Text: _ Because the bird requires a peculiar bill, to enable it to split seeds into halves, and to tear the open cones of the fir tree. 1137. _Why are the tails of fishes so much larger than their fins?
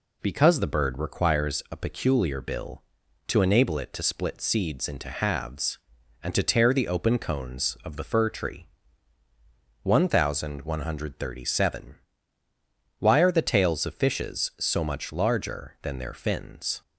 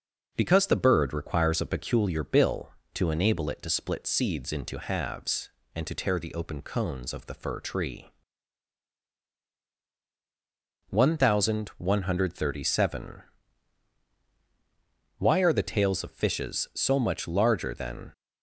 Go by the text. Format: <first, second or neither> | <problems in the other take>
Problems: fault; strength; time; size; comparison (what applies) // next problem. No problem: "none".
first | stops before "their fins"; at 18.1 s